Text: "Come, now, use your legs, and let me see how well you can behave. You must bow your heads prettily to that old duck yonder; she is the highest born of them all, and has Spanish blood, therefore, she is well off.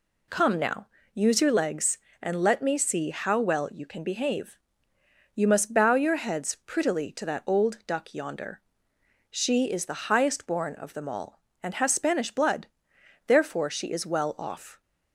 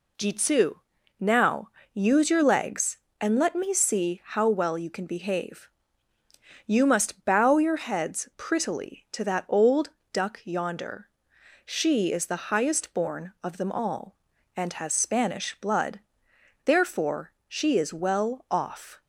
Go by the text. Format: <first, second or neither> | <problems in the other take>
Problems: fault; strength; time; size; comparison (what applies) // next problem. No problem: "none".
first | says "Jitsu" for "Come"; at 0.1 s // pauses between "old" and "duck"; slight; at 9.8 s; 0.22 s long